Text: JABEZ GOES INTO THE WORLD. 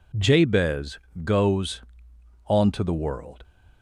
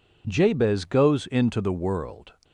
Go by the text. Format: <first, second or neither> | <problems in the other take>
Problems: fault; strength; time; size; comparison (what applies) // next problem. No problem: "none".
second | pauses between "JABEZ" and "GOES"; slight; at 0.9 s; 0.26 s long // says "Onto" for "INTO"; at 2.4 s